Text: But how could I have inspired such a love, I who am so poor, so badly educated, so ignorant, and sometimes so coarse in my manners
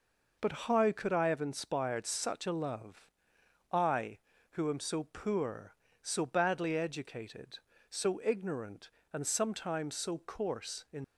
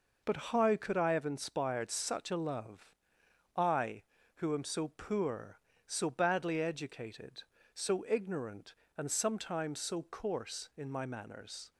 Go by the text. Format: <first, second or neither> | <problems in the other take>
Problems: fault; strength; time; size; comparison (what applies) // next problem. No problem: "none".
second | stops before "my manners"; at 11.0 s